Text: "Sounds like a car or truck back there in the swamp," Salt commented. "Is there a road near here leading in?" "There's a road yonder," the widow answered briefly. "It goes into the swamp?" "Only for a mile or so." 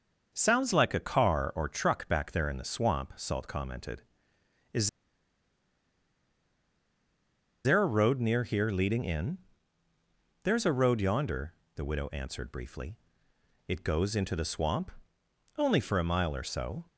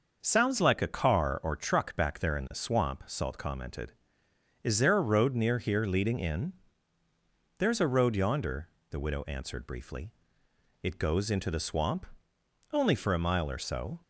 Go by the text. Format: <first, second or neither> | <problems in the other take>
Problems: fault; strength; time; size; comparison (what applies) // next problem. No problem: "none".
second | starts louder than the rest; noticeable; until 1.3 s; 6 dB; noticeable in the second // pauses between "Is" and "there"; strong; at 4.8 s; 2.7 s long